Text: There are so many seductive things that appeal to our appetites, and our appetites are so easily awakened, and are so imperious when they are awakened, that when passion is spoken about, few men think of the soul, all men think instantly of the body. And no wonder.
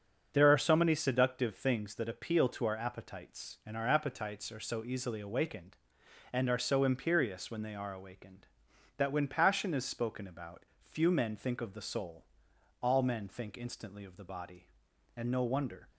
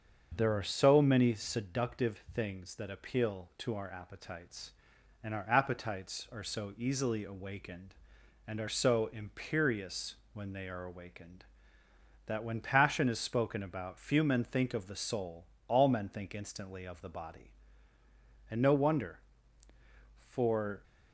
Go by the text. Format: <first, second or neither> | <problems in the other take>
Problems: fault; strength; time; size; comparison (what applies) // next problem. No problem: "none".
first | starts louder than the rest; until 1.3 s; 6.5 dB; also in the first // pauses between "imperious" and "when"; slight; at 10.1 s; 0.18 s long // goes on to say "For"; from 20.2 s on; 0.56 s long